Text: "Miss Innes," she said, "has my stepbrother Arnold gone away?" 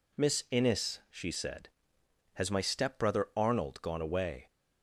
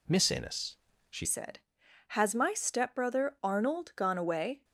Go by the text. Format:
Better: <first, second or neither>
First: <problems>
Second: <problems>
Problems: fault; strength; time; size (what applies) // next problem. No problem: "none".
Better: first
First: none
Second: changes voice at "said"; from 1.2 s on; 3.4 s long